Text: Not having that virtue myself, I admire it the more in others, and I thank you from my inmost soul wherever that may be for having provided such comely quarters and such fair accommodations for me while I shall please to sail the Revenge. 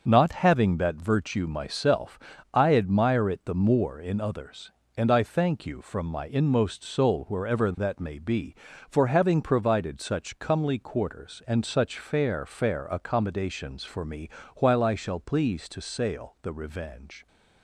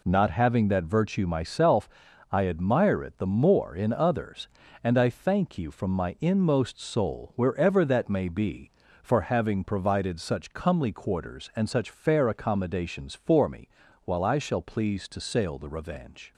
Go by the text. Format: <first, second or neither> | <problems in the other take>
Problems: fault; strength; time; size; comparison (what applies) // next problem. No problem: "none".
second | starts louder than the rest; until 1.0 s; 6 dB // says "fair" twice; at 12.4 s // pauses between "me" and "while"; slight; at 14.3 s; 0.26 s long; slight in the second